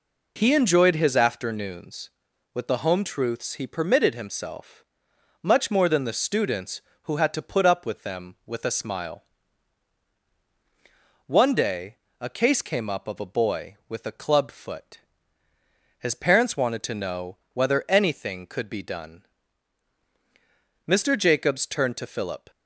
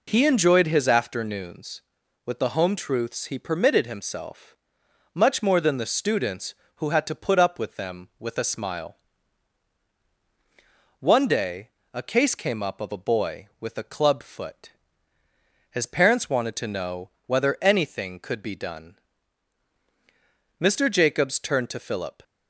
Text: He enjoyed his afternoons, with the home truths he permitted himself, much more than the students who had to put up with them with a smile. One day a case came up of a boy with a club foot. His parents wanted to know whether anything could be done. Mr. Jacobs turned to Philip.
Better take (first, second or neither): neither